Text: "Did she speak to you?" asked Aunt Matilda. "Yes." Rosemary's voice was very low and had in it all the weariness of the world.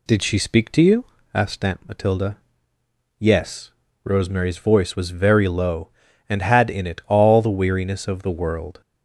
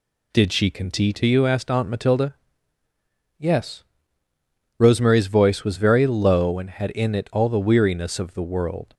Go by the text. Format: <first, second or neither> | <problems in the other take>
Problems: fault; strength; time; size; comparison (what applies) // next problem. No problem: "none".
first | says "conti" for "speak"; at 0.7 s